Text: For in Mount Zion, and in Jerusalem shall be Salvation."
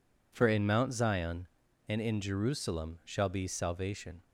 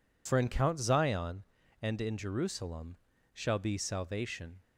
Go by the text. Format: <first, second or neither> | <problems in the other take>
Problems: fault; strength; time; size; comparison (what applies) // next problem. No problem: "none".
first | says "Count" for "Mount"; at 0.4 s // pauses between "Jerusalem" and "shall"; slight; at 2.9 s; 0.36 s long